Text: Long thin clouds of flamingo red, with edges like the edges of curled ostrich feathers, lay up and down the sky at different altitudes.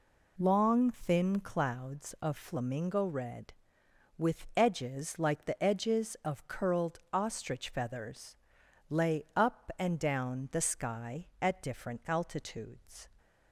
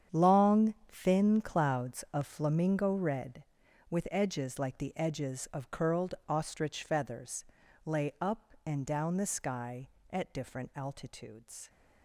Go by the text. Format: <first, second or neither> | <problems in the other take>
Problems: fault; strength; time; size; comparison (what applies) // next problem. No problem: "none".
first | gets quieter; strong; throughout; 15.5 dB // pauses between "Long" and "thin"; slight; at 0.7 s; 0.18 s long